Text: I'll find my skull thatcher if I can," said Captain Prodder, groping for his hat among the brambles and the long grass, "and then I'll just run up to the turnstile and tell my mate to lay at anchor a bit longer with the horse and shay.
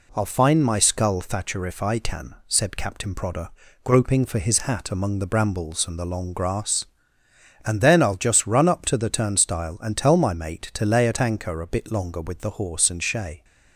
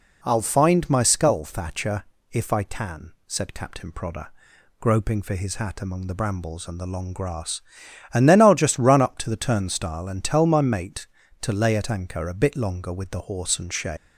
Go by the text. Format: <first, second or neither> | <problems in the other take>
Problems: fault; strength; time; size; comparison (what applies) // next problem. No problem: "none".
first | pauses between "thatcher" and "if"; slight; at 2.0 s; 0.28 s long // leaves "shay" unfinished; at 13.9 s; 165 ms